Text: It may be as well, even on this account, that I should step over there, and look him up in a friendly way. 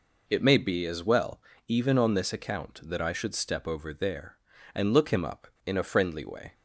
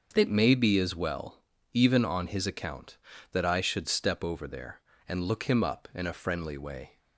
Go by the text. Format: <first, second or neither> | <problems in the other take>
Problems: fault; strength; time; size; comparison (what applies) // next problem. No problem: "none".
first | starts louder than the rest; until 1.1 s; 6.5 dB // says "his" for "this"; at 2.2 s